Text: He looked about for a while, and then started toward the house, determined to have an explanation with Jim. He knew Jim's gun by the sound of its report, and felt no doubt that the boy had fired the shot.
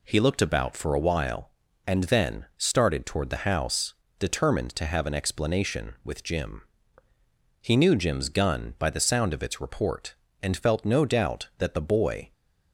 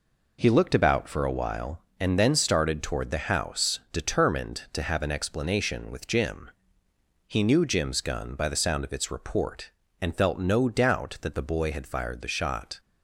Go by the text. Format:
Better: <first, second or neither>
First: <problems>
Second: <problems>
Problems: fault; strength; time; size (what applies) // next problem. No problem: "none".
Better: second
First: stops before "had fired the shot"; at 12.3 s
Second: none